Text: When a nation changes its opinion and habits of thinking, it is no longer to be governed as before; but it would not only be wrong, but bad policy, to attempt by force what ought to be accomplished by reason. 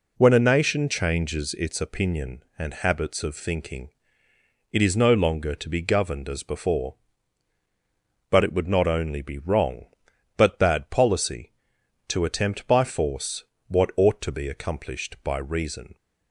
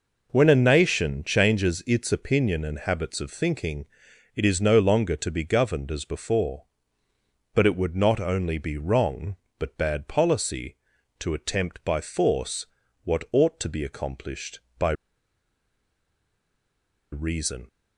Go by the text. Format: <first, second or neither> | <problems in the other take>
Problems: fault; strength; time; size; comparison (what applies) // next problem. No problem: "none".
first | pauses between "force" and "what"; slight; at 12.6 s; 0.36 s long; slight in the first // pauses between "by" and "reason"; strong; at 14.9 s; 2.1 s long